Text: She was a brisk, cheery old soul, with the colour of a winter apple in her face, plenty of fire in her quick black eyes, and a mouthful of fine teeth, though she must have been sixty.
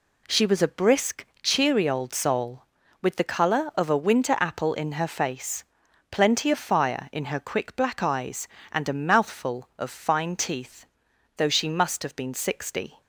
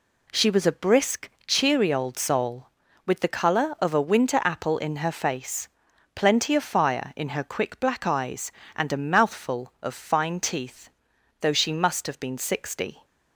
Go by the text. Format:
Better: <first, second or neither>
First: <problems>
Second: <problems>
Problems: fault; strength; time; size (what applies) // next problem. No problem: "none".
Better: neither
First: none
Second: none